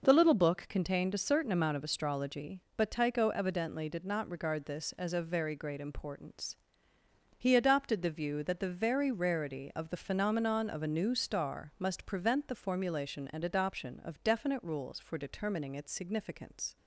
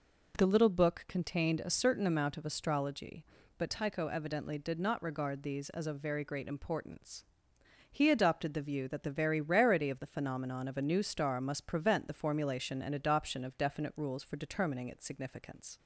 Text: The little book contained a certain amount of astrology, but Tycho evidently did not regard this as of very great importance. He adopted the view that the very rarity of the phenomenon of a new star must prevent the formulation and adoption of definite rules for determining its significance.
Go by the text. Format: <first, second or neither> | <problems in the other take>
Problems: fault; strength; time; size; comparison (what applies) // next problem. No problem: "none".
first | says "these" for "this"; at 5.4 s